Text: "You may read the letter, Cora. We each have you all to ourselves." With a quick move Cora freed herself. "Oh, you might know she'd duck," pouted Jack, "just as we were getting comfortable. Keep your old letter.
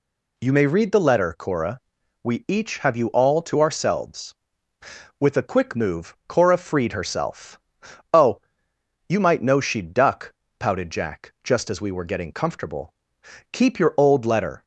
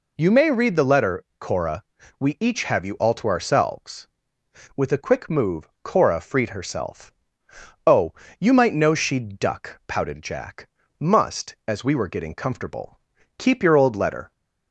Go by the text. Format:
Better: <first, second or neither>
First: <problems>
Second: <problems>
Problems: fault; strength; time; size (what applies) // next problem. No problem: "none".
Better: first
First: none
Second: pauses between "move" and "Cora"; slight; at 5.6 s; 0.16 s long // says "must" for "just"; at 10.9 s